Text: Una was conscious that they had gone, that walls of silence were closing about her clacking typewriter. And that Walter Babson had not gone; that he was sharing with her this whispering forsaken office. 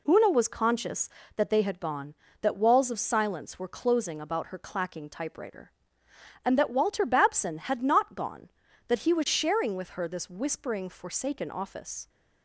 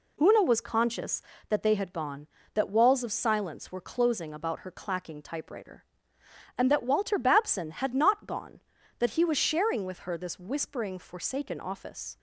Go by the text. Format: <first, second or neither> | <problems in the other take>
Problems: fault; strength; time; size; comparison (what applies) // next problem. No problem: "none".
neither | none